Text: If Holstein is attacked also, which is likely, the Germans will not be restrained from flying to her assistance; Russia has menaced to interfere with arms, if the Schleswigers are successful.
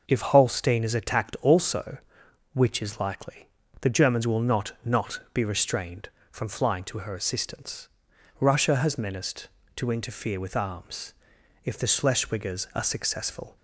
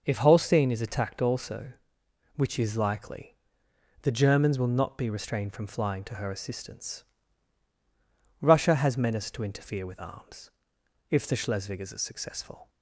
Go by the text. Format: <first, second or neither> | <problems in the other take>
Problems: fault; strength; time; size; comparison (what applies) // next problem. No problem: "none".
second | says "not" twice; at 4.8 s